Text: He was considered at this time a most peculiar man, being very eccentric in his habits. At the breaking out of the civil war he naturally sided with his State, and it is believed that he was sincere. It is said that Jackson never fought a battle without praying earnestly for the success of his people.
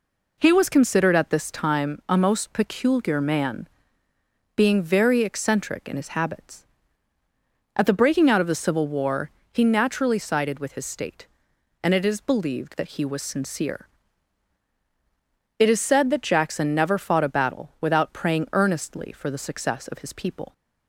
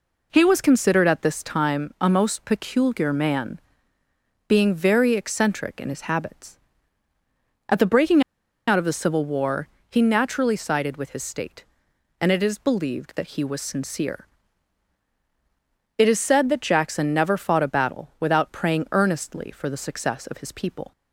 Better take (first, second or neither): first